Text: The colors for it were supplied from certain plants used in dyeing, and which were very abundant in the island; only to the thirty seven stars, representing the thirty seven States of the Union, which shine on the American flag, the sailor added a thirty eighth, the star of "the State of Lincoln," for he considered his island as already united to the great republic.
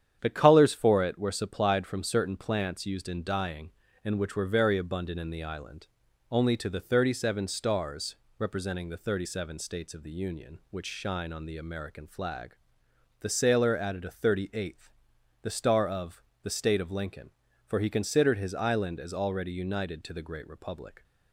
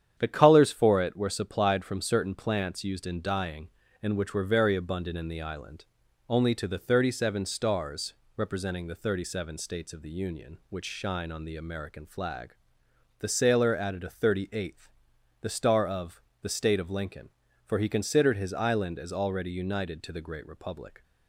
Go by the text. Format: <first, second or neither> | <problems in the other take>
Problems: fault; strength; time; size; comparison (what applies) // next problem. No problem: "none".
neither | starts louder than the rest; strong; the same in both // pauses between "of" and "the"; slight; the same in both